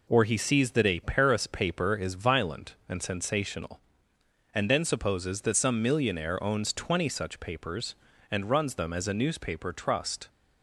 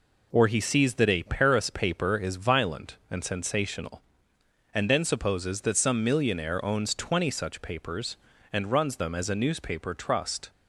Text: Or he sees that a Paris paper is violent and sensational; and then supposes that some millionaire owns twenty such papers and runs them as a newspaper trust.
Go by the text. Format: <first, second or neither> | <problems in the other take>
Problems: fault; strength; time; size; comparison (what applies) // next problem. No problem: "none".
neither | none